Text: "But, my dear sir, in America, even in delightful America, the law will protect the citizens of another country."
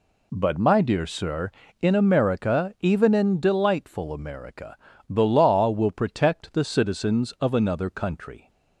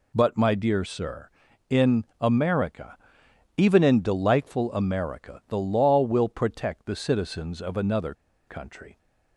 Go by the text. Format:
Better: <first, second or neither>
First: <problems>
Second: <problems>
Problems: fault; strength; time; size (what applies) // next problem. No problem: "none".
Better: first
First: none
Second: pauses between "in" and "America"; slight; at 2.0 s; 0.16 s long // pauses between "another" and "country"; slight; at 8.1 s; 0.34 s long